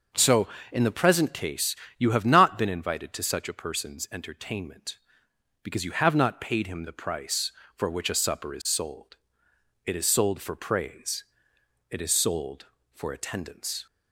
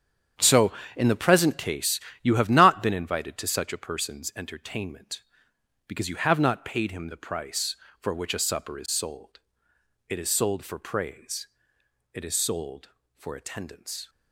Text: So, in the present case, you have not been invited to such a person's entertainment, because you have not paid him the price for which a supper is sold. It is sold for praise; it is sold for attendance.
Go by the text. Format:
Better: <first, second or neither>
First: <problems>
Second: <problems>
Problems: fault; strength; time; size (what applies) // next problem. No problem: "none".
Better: first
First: none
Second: gets quieter; strong; throughout; 11 dB